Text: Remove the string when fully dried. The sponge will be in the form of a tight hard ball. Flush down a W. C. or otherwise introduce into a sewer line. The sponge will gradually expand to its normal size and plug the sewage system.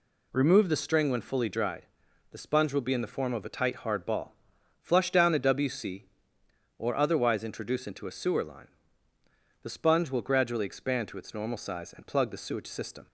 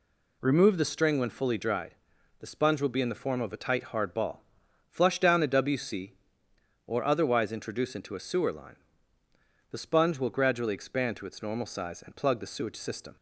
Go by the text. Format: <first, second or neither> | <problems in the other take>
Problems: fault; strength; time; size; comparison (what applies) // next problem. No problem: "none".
neither | none